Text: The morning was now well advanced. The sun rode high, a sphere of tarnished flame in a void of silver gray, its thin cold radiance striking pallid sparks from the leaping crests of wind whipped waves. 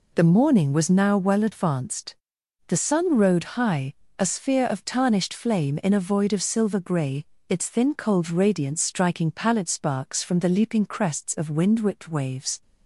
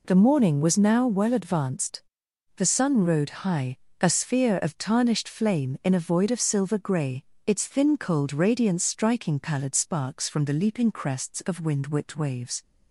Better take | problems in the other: neither | none

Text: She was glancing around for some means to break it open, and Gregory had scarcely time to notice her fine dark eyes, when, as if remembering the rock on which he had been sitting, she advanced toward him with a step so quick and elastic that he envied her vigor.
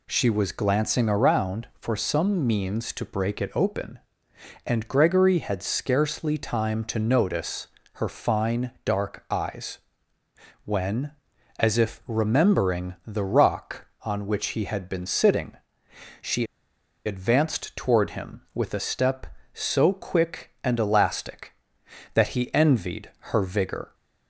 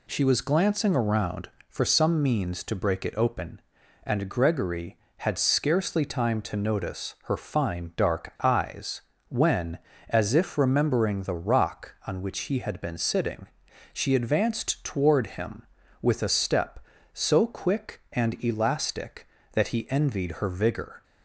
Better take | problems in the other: second | pauses between "notice" and "her"; slight; at 7.6 s; 0.26 s long // pauses between "she" and "advanced"; noticeable; at 16.4 s; 0.61 s long

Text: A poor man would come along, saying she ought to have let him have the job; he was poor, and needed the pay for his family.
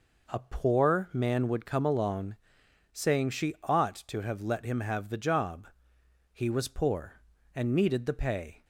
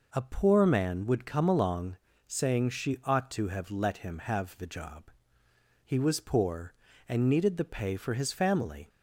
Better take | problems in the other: second | stops before "for his family"; at 8.6 s

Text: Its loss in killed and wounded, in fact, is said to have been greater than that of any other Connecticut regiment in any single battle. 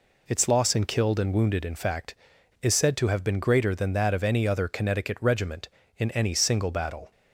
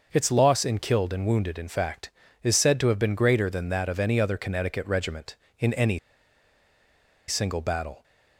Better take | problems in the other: first | starts louder than the rest; noticeable; until 1.1 s; 6 dB // pauses between "any" and "single"; strong; at 5.9 s; 1.3 s long

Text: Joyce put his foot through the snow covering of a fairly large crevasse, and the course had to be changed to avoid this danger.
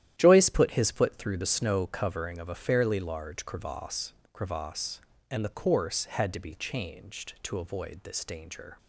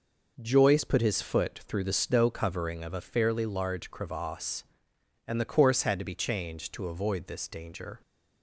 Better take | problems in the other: second | starts louder than the rest; strong; until 1.1 s; 11.5 dB // says "crevasse" twice; at 4.3 s

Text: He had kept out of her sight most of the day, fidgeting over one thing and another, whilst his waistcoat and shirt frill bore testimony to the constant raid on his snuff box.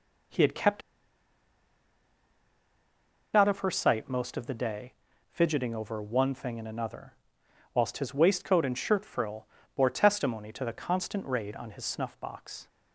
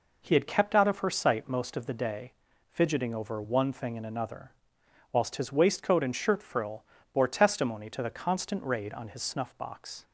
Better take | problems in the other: second | pauses between "kept" and "out"; strong; at 0.8 s; 2.5 s long // pauses between "frill" and "bore"; slight; at 9.4 s; 0.30 s long; slight in the second

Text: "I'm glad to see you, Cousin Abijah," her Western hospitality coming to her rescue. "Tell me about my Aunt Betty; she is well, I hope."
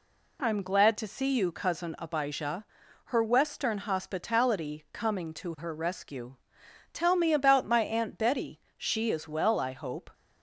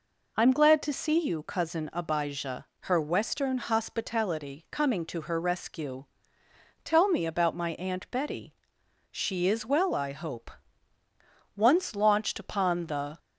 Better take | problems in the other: first | goes on to say "Once launched upon the"; from 11.5 s on; 1.6 s long

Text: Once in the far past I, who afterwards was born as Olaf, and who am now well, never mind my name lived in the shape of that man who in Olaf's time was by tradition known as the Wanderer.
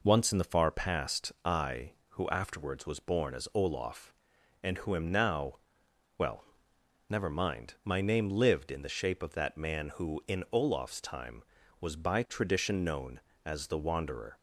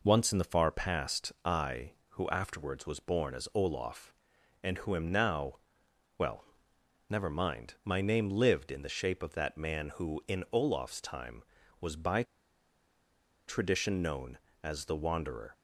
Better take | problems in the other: first | pauses between "now" and "well"; noticeable; at 5.5 s; 0.60 s long; noticeable in the first // pauses between "by" and "tradition"; at 12.2 s; 1.2 s long

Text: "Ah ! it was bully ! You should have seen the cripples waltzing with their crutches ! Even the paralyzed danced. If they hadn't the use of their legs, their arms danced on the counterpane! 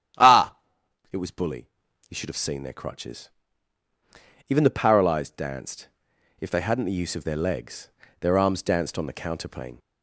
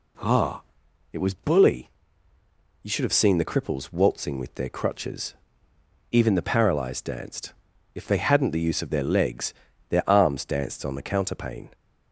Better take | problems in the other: second | starts louder than the rest; strong; until 2.1 s; 11 dB // skips "the cripples waltzing with"; at 2.6 s

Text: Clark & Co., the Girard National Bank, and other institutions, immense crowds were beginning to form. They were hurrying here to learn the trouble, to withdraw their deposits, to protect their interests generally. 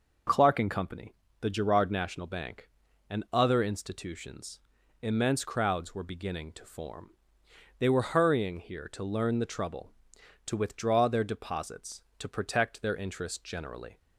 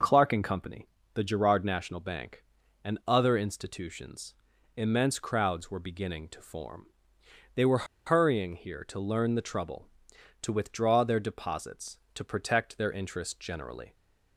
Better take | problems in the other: first | pauses between "were" and "hurrying"; slight; at 7.8 s; 0.22 s long

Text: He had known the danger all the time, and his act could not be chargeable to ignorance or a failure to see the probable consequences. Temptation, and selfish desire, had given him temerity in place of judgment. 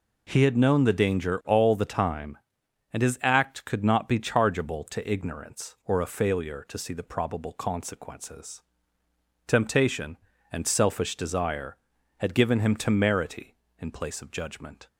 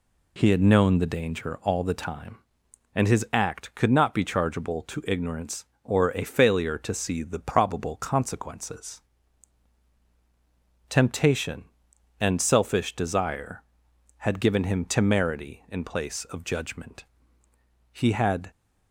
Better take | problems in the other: first | goes on to say "He had"; from 17.9 s on; 0.60 s long

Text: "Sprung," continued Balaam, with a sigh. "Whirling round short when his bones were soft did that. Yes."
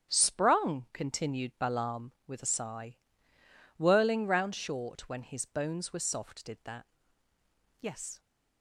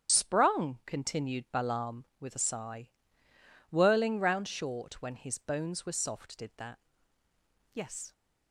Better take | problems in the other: first | loses the start of "Sprung"; at 0.0 s; 60 ms // starts louder than the rest; strong; until 1.1 s; 8.5 dB; strong in the first

